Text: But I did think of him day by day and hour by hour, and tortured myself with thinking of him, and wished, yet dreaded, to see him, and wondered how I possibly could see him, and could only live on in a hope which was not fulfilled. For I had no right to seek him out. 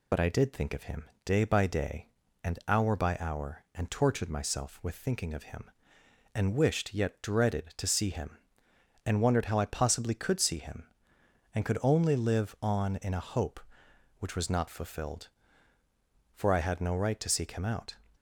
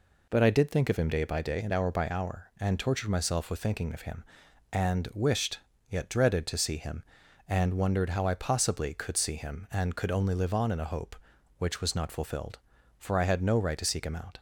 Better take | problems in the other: second | loses the start of "But"; at 0.1 s; 40 ms // pauses between "him" and "day"; slight; at 1.0 s; 0.16 s long

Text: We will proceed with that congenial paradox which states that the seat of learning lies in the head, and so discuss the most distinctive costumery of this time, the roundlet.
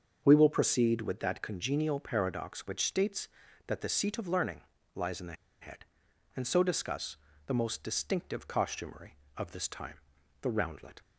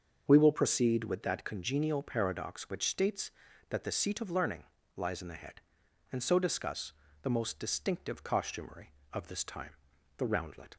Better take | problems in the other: second | starts louder than the rest; until 1.2 s; 6.5 dB; also in the second // pauses between "learning" and "lies"; slight; at 4.6 s; 0.34 s long; slight in the second // pauses between "the" and "head"; slight; at 5.3 s; 0.28 s long // pauses between "discuss" and "the"; slight; at 7.1 s; 0.30 s long; slight in the second

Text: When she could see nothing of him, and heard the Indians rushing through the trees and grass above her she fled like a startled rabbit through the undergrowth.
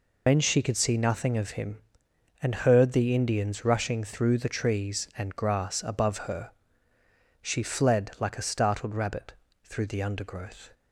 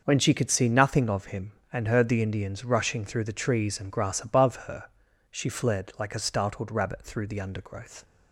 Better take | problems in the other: second | loses the start of "When"; at 0.2 s; 120 ms // pauses between "her" and "she"; noticeable; at 6.5 s; 0.90 s long; noticeable in the second // pauses between "rabbit" and "through"; slight; at 9.3 s; 0.30 s long

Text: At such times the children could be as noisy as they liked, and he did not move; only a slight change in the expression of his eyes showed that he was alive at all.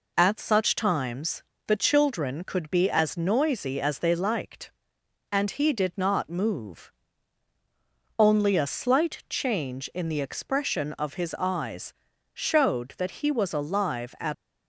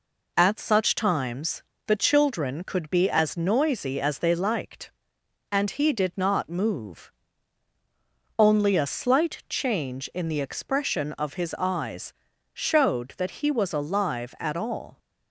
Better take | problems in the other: second | pauses between "times" and "the"; slight; at 1.4 s; 0.24 s long; slight in the second // pauses between "eyes" and "showed"; at 11.9 s; 0.42 s long; also in the second // stops before "all"; at 14.3 s

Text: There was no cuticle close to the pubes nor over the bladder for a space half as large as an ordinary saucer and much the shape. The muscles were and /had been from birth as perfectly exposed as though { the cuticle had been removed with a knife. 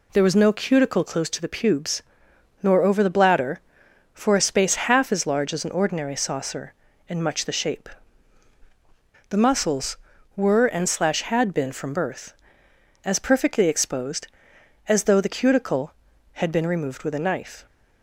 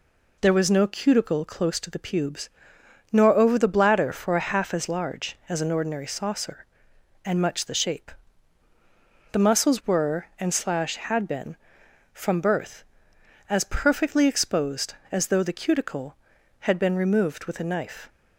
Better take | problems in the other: first | pauses between "pubes" and "nor"; noticeable; at 2.4 s; 0.62 s long; noticeable in the first // skips "space"; at 4.4 s

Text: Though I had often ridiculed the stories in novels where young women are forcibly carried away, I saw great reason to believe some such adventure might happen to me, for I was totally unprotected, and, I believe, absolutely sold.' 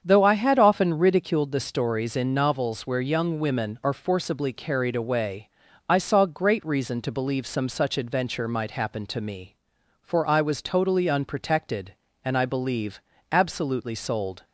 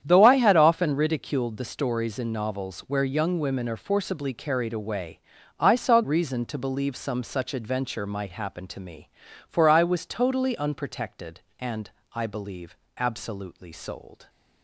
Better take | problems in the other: first | starts louder than the rest; strong; until 1.0 s; 9 dB; strong in the first // skips "great"; at 6.0 s

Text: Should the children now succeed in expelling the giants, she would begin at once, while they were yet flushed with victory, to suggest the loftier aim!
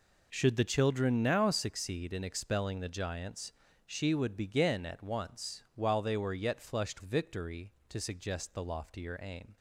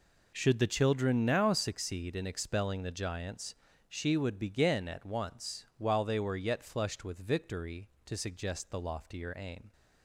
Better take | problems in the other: second | skips "with"; at 7.0 s

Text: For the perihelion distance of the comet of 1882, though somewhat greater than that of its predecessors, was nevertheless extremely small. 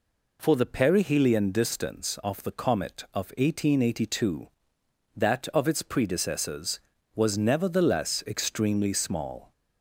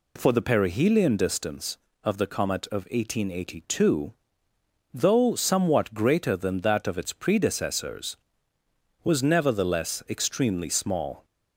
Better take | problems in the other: second | skips "though somewhat greater than"; at 4.8 s

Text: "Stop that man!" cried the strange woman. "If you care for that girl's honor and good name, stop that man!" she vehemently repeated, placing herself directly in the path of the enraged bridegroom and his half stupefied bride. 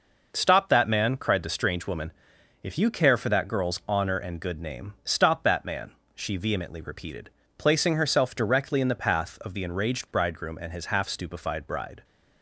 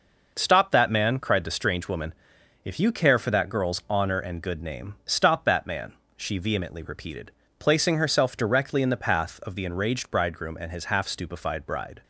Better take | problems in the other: neither | none

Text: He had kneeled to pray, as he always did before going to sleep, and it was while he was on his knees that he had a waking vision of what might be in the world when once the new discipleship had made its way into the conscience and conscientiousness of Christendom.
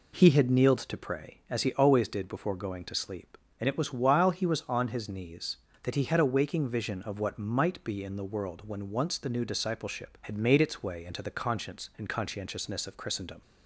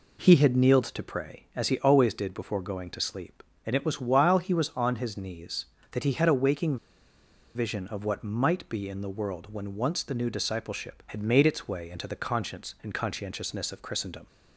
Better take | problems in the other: first | pauses between "waking" and "vision"; noticeable; at 6.7 s; 0.79 s long

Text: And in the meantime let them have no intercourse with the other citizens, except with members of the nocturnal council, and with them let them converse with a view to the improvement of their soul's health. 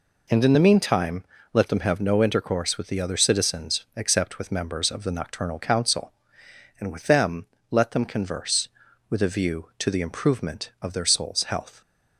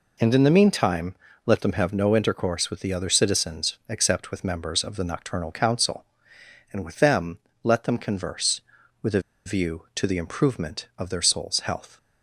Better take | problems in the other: first | pauses between "meantime" and "let"; slight; at 1.1 s; 0.32 s long; slight in the first // pauses between "them" and "let"; slight; at 7.3 s; 0.26 s long; slight in the first // pauses between "a" and "view"; slight; at 9.2 s; 0.24 s long

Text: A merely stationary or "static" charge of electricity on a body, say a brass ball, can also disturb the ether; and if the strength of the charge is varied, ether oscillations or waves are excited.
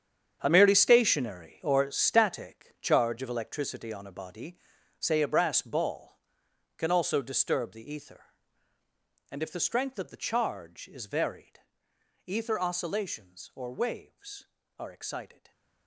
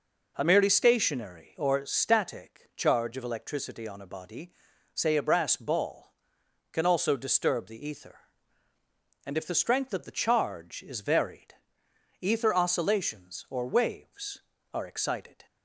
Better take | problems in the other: second | gets quieter; strong; throughout; 13 dB

